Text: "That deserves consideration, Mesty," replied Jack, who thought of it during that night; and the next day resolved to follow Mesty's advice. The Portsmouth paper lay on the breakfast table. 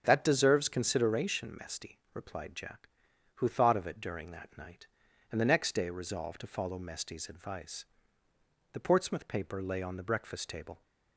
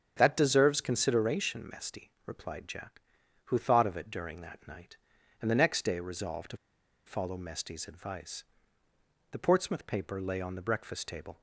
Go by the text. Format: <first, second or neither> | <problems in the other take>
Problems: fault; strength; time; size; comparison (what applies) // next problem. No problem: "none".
first | starts louder than the rest; strong; until 1.1 s; 7.5 dB; strong in the first // pauses between "to" and "follow"; noticeable; at 6.5 s; 0.48 s long